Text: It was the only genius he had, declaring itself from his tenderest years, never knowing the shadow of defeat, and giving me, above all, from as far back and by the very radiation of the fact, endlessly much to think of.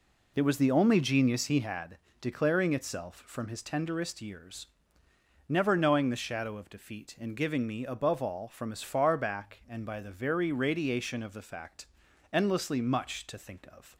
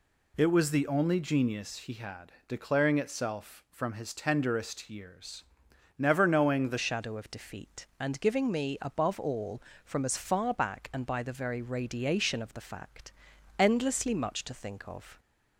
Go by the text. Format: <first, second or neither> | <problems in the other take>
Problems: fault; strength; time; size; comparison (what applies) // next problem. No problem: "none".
first | changes voice at "shadow"; from 6.7 s on; 8.4 s long